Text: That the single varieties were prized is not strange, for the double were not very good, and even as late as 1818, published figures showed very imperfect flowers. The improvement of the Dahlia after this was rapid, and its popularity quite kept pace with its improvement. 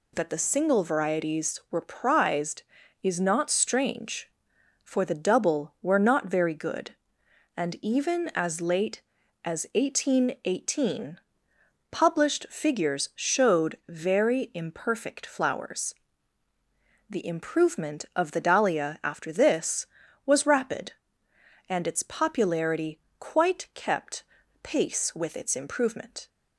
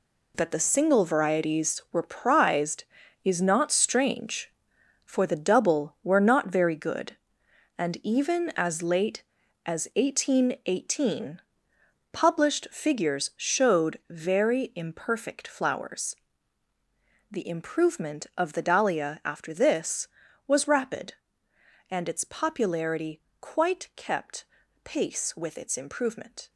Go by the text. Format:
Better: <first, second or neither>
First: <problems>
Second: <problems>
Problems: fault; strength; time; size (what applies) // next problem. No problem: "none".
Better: first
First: pauses between "popularity" and "quite"; slight; at 23.0 s; 0.18 s long // pauses between "kept" and "pace"; at 24.2 s; 0.40 s long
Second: gets quieter; strong; throughout; 9.5 dB // pauses between "popularity" and "quite"; slight; at 23.2 s; 0.18 s long // pauses between "kept" and "pace"; at 24.4 s; 0.40 s long